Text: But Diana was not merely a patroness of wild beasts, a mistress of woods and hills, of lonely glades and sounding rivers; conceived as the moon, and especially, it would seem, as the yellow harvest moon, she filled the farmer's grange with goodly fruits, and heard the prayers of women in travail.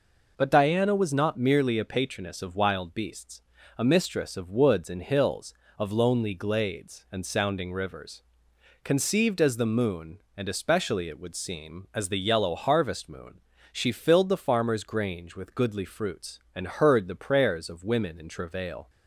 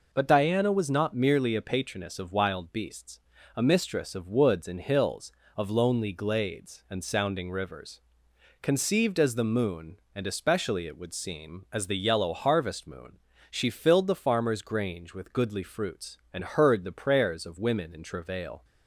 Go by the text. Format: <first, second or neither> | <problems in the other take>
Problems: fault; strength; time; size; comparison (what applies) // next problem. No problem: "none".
neither | none